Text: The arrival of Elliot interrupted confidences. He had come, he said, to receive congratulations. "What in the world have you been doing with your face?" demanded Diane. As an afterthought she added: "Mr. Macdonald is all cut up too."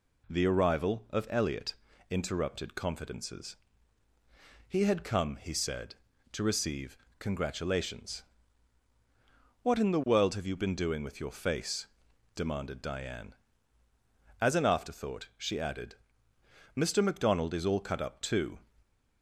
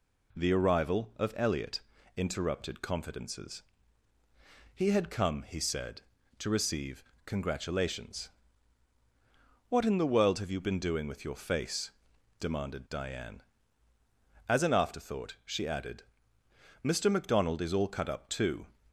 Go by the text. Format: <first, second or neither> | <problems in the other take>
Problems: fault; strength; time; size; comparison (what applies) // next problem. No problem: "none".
neither | pauses between "Elliot" and "interrupted"; slight; the same in both // pauses between "receive" and "congratulations"; slight; the same in both